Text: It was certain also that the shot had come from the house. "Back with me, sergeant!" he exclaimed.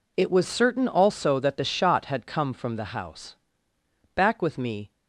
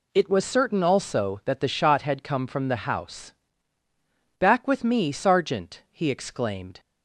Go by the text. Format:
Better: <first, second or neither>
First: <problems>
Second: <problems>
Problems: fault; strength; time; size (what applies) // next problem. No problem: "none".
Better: second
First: stops before "sergeant he exclaimed"; at 4.9 s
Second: none